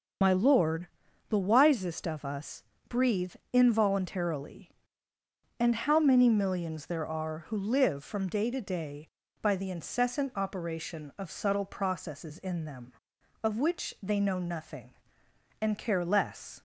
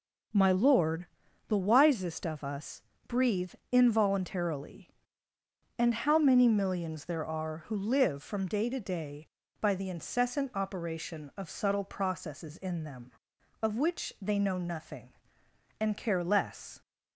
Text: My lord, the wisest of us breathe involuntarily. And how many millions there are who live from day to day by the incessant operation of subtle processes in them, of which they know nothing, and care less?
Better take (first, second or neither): second